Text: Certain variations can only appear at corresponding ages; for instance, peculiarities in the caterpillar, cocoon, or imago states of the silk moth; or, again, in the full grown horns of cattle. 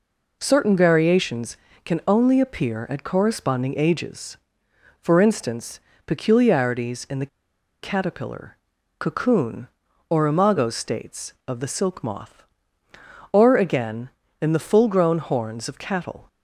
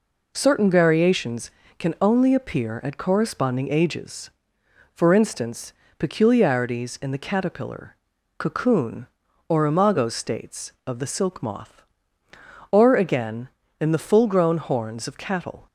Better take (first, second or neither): second